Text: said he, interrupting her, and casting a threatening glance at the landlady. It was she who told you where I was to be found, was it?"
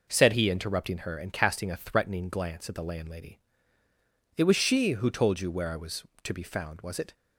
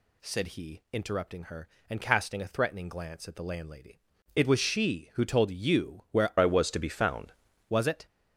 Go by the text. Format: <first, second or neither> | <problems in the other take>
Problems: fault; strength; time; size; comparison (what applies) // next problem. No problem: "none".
first | changes voice from "I" to "found"; from 6.3 to 7.3 s; 1.0 s long